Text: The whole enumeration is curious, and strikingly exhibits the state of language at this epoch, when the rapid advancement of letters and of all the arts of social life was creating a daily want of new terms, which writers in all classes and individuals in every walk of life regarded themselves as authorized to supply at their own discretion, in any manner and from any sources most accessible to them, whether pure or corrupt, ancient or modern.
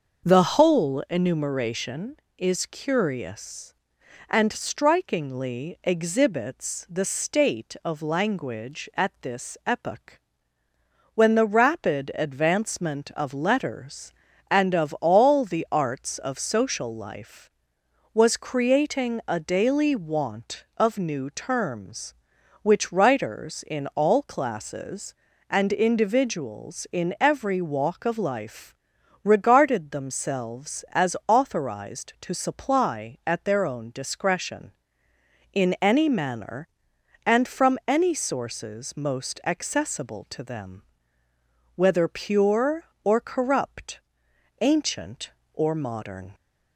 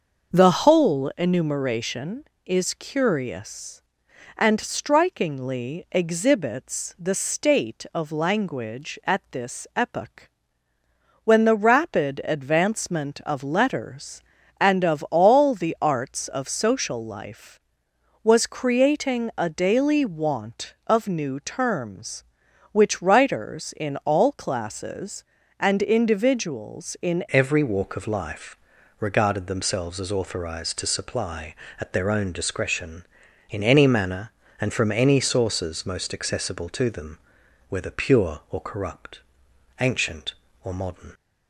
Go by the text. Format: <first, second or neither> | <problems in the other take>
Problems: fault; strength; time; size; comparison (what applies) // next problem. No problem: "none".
first | starts louder than the rest; until 1.3 s; 6 dB; also in the first // changes voice at "every"; from 27.3 s on; 13.8 s long // pauses between "life" and "regarded"; at 28.5 s; 0.44 s long; noticeable in the first